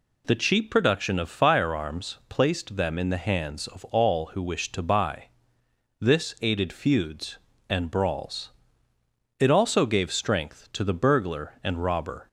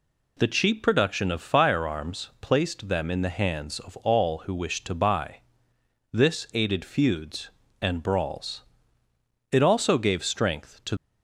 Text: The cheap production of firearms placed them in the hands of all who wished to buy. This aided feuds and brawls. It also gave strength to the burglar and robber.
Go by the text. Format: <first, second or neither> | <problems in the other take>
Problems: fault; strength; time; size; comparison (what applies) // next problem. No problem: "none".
first | stops before "the burglar and robber"; at 10.9 s